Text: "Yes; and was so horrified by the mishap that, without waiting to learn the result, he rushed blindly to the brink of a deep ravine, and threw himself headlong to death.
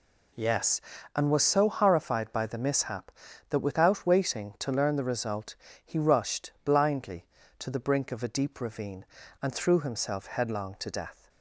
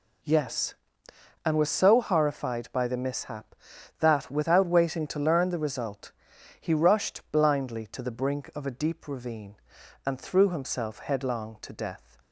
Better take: neither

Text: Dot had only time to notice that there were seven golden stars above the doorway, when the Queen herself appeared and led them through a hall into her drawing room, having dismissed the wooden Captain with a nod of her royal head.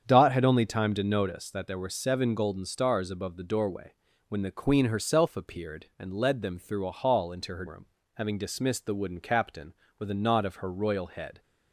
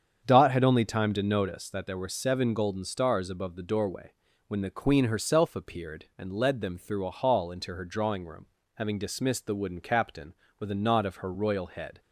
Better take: second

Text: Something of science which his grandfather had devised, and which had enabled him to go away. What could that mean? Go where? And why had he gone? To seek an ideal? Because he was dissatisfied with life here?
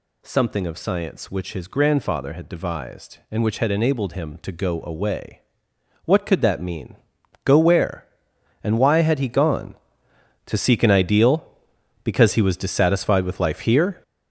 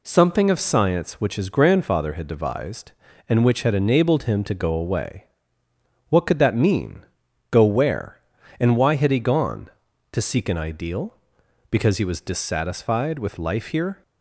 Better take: second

